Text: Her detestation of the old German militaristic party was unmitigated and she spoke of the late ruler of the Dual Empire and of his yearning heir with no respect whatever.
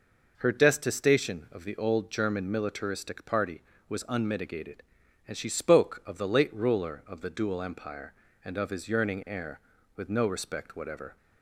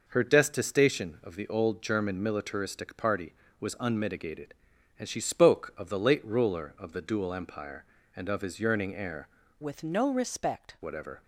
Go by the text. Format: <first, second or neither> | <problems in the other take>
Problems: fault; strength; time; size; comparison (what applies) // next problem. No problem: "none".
first | changes voice from "with" to "respect"; from 9.6 to 10.7 s; 1.1 s long